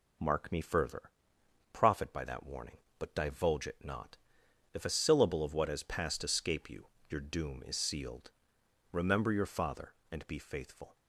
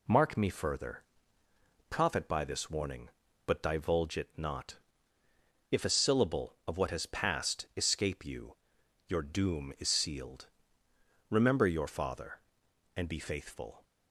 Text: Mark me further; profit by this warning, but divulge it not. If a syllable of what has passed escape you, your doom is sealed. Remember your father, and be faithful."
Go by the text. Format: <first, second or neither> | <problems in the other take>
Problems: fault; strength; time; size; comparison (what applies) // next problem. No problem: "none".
second | says "that" for "this"; at 2.2 s